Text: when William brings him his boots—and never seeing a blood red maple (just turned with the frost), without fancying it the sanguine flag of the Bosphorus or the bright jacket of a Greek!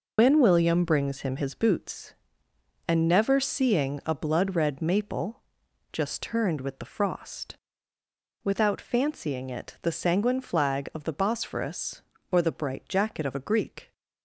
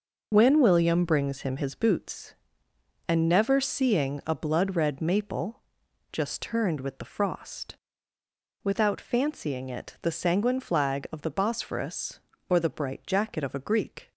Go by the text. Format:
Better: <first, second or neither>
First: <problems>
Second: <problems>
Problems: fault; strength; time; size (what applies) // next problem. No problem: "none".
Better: second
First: loses the start of "when"; at 0.1 s; 70 ms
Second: none